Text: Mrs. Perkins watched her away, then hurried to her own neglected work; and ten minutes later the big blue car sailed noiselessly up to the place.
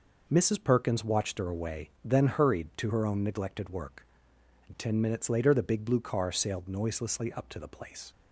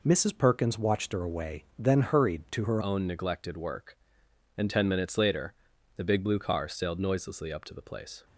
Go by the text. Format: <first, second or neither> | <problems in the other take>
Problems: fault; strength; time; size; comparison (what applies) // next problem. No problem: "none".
first | changes voice at "own"; from 2.8 s on; 5.4 s long // pauses between "later" and "the"; at 5.5 s; 0.42 s long